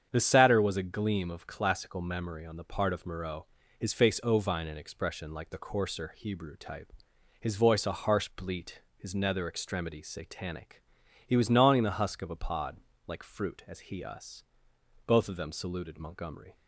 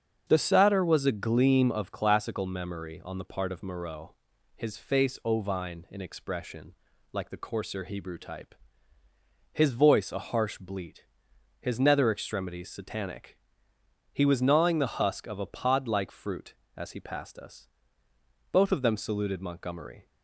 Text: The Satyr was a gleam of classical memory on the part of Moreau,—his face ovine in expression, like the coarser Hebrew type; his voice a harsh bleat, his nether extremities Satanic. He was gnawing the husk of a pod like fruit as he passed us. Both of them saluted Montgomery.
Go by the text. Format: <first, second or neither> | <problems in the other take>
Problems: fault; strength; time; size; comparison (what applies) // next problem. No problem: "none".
second | starts louder than the rest; strong; until 1.1 s; 8 dB; also in the second // pauses between "pod" and "like"; slight; at 12.7 s; 0.30 s long // skips "passed"; at 14.0 s